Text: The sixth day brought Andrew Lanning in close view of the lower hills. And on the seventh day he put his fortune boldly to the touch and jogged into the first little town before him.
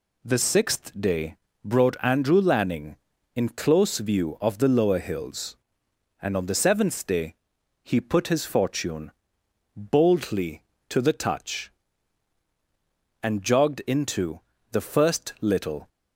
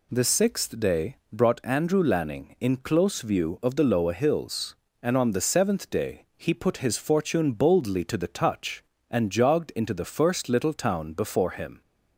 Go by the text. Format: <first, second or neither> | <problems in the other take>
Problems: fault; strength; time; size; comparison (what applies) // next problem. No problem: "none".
second | pauses between "day" and "brought"; slight; at 1.3 s; 0.28 s long; slight in the second // pauses between "day" and "he"; noticeable; at 7.3 s; 0.46 s long // pauses between "fortune" and "boldly"; noticeable; at 9.1 s; 0.64 s long // pauses between "into" and "the"; slight; at 14.4 s; 0.32 s long // stops before "town before him"; at 15.8 s